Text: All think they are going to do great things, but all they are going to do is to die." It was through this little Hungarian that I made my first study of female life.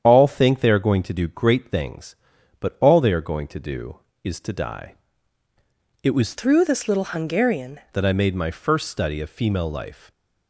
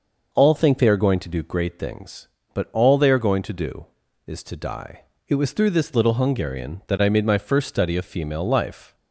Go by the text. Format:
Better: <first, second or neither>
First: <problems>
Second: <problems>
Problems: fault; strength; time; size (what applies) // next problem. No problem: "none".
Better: second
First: starts louder than the rest; strong; until 1.0 s; 8.5 dB // changes voice from "through" to "Hungarian"; from 6.3 to 7.7 s; 1.4 s long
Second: none